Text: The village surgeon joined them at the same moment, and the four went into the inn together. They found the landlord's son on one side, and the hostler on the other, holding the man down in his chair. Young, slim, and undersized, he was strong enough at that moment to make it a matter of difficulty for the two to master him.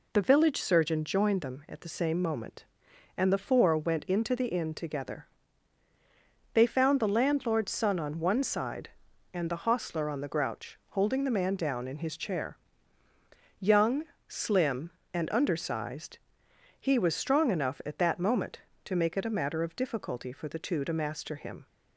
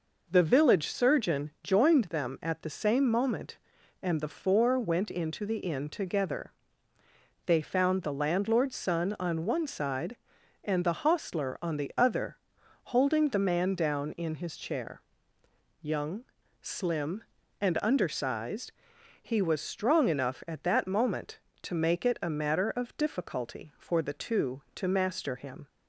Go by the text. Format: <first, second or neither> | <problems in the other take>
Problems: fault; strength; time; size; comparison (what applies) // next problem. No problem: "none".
second | says "grouch" for "other"; at 10.2 s